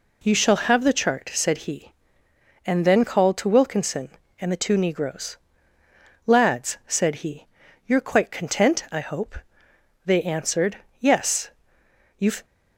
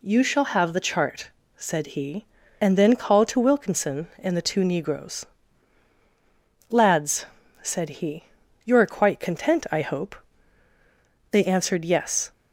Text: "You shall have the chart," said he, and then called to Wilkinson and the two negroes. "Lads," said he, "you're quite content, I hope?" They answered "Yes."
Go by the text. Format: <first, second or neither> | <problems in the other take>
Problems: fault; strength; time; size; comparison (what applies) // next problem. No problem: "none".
second | pauses between "answered" and "Yes"; slight; at 10.7 s; 0.24 s long // goes on to say "You've"; slight; from 12.1 s on; 0.26 s long